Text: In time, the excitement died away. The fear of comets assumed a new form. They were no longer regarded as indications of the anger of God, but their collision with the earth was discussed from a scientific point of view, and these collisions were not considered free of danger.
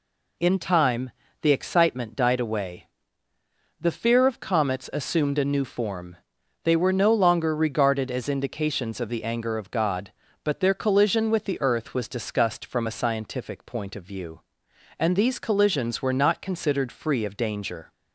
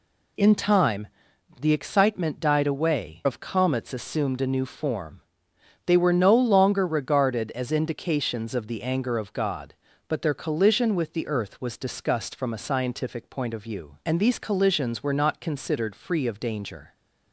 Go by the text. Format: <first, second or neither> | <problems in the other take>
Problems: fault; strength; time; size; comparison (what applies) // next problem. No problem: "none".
first | skips "The fear"; at 3.2 s